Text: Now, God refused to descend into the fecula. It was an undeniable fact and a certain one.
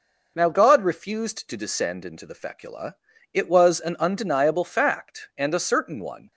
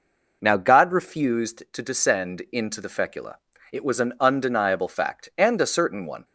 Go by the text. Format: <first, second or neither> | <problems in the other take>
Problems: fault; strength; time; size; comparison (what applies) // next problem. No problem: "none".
neither | none